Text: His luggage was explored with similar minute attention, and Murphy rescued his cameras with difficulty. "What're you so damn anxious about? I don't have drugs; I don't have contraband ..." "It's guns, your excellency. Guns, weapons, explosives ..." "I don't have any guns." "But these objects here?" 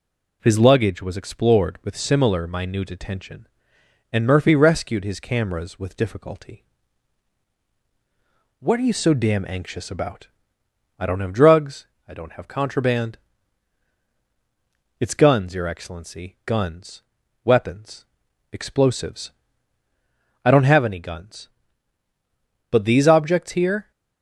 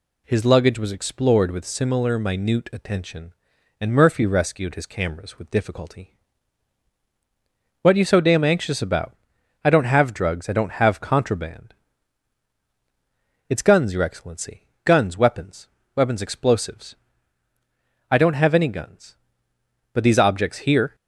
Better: first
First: none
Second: says "weapons" twice; at 15.9 s

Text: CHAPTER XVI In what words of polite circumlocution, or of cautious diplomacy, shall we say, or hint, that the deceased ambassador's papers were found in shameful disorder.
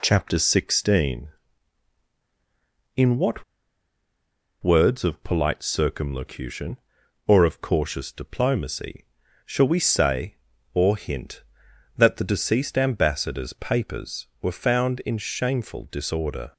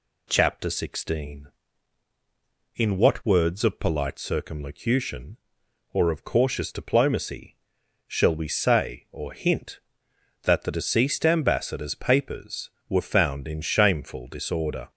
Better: second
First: pauses between "what" and "words"; at 3.4 s; 1.1 s long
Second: none

